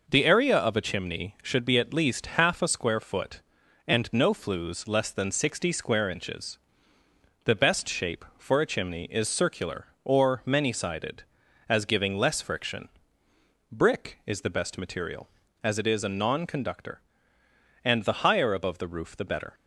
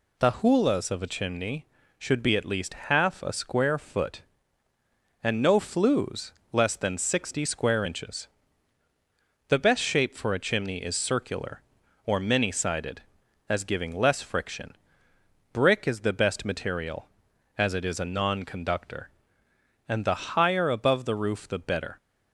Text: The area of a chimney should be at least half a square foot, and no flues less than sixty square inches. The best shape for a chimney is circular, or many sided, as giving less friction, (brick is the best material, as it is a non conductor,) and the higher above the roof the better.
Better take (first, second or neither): first